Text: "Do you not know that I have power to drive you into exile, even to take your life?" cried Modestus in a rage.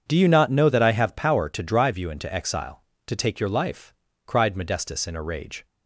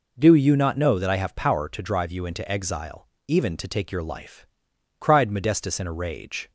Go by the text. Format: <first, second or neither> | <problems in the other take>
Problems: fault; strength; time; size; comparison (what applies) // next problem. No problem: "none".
second | starts louder than the rest; strong; until 1.0 s; 7 dB // skips "even"; at 2.9 s